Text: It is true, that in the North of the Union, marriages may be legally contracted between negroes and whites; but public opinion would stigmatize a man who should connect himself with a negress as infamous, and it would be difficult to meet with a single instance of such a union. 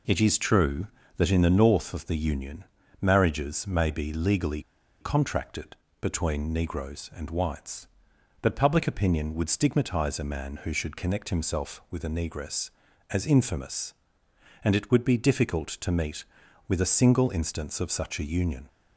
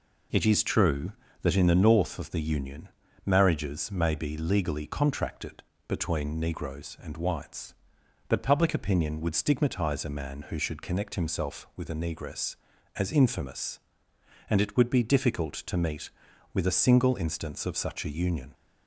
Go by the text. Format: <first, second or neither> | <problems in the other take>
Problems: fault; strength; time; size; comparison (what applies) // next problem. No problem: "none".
second | pauses between "legally" and "contracted"; at 4.6 s; 0.38 s long // pauses between "contracted" and "between"; slight; at 5.7 s; 0.26 s long; slight in the second